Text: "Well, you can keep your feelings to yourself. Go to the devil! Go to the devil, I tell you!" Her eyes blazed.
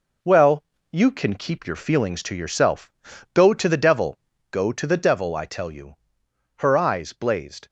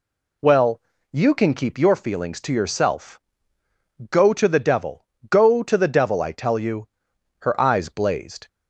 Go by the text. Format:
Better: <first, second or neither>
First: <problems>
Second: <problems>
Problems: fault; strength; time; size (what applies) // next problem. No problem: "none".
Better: second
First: gets quieter; noticeable; throughout; 5.5 dB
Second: none